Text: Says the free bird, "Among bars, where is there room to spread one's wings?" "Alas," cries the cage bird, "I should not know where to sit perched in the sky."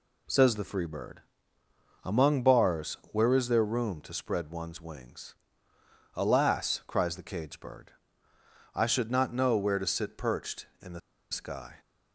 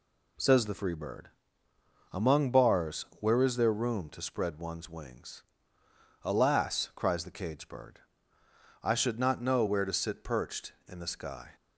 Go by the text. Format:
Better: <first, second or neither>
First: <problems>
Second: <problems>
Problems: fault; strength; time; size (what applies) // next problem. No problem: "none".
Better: second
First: pauses between "the" and "sky"; slight; at 11.0 s; 0.32 s long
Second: none